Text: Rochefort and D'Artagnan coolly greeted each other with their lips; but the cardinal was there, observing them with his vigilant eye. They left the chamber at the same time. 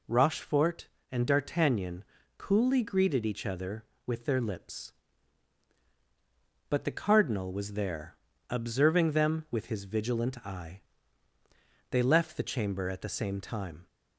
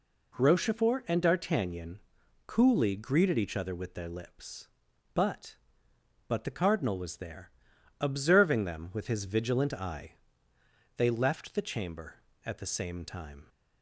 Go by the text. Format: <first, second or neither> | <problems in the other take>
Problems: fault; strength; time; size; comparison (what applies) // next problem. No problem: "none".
first | pauses between "D'Artagnan" and "coolly"; noticeable; at 1.9 s; 0.48 s long; slight in the first // says "but" twice; at 6.2 s